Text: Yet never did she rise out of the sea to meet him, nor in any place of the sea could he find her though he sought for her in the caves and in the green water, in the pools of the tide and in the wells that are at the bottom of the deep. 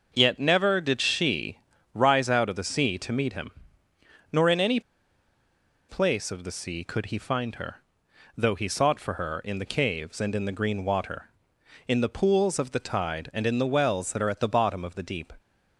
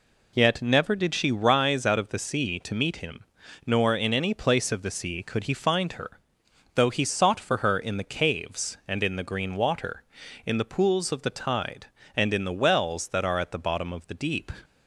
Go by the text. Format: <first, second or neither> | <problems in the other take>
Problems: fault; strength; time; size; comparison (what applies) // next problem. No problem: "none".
second | pauses between "she" and "rise"; slight; at 1.5 s; 0.36 s long // pauses between "any" and "place"; at 4.7 s; 1.0 s long // pauses between "her" and "though"; noticeable; at 7.8 s; 0.58 s long; noticeable in the second